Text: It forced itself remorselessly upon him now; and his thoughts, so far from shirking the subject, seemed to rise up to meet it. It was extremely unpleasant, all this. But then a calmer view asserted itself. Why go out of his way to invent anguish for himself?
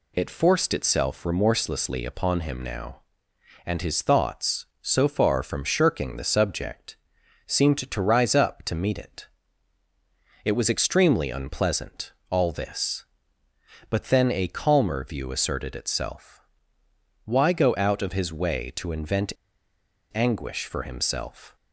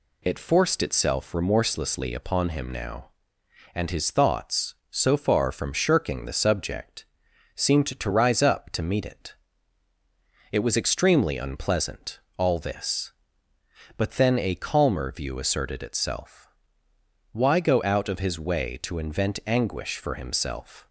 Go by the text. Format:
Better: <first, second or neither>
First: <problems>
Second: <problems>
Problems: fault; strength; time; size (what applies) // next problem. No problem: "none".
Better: second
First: pauses between "invent" and "anguish"; noticeable; at 19.3 s; 0.82 s long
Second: none